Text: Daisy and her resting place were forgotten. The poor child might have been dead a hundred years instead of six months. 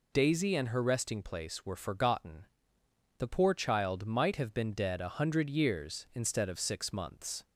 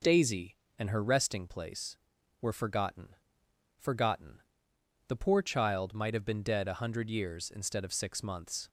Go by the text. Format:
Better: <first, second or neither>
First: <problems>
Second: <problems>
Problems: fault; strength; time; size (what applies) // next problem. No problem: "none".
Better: first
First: none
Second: says "forgotten" twice; at 3.7 s